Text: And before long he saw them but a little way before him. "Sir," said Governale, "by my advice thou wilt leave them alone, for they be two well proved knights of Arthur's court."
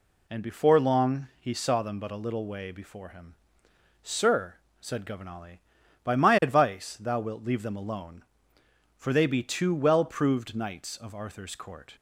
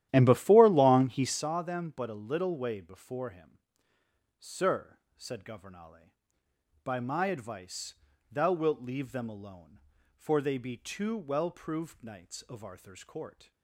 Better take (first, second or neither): first